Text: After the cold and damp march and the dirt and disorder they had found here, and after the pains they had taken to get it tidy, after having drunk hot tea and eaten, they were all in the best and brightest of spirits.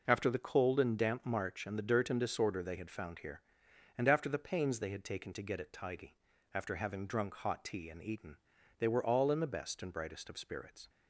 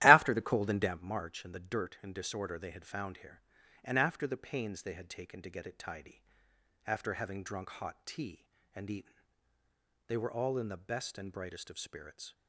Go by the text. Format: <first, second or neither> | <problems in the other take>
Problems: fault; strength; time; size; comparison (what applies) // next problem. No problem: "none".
first | starts louder than the rest; strong; until 1.1 s; 14.5 dB